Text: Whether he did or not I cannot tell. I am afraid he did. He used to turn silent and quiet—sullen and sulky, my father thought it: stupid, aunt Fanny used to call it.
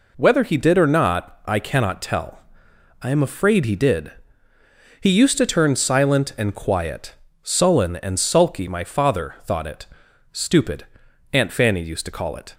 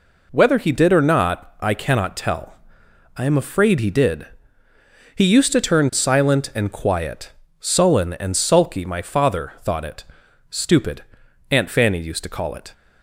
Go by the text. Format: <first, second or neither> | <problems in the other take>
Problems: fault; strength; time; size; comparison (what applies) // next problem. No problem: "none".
neither | none